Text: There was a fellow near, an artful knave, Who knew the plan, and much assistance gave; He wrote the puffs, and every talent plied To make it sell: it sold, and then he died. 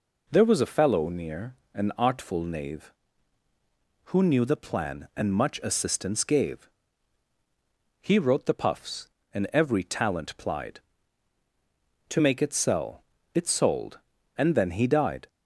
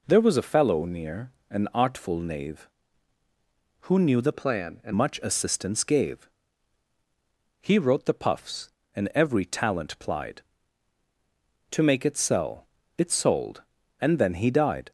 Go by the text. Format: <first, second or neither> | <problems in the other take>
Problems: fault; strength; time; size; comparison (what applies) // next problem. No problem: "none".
first | changes voice from "plan" to "and"; from 4.3 to 4.9 s; 0.6 s long